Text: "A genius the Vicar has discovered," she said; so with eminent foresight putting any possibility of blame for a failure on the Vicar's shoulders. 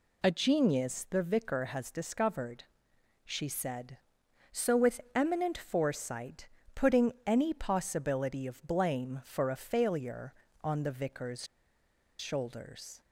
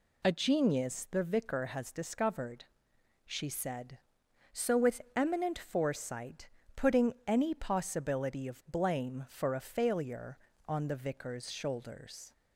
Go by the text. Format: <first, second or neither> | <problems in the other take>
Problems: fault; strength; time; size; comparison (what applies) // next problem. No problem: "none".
second | pauses between "with" and "eminent"; slight; at 4.9 s; 0.16 s long; slight in the second // pauses between "foresight" and "putting"; slight; at 6.4 s; 0.28 s long; slight in the second // pauses between "Vicar's" and "shoulders"; noticeable; at 11.4 s; 0.73 s long